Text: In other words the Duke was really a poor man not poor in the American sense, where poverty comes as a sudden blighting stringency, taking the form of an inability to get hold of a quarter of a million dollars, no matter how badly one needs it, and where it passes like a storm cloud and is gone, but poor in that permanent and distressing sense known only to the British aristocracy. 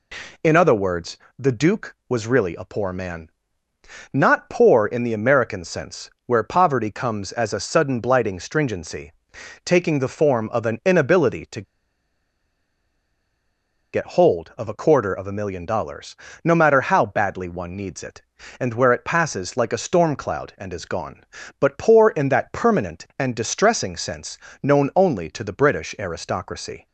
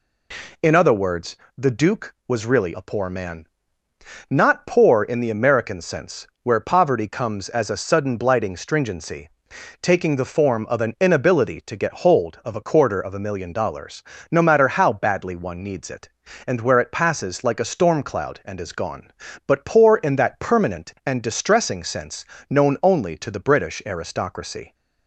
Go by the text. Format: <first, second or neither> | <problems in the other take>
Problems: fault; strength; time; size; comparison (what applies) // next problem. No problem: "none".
second | pauses between "words" and "the"; slight; at 1.1 s; 0.22 s long; slight in the second // pauses between "man" and "not"; noticeable; at 3.3 s; 0.82 s long; noticeable in the second // pauses between "to" and "get"; strong; at 11.6 s; 2.3 s long // pauses between "sense" and "known"; slight; at 24.3 s; 0.24 s long; slight in the second